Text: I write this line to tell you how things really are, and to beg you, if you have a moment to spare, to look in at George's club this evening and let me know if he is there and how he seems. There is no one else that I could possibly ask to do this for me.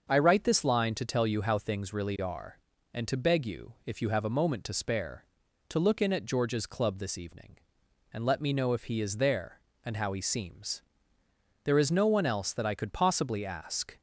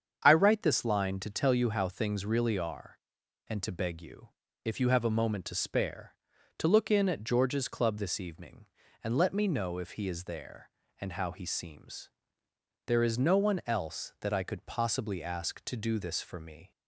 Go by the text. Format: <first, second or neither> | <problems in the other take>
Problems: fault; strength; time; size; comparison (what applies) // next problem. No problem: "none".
second | starts louder than the rest; until 1.0 s; 6.5 dB; strong in the second // stops before "to do this for me"; at 13.9 s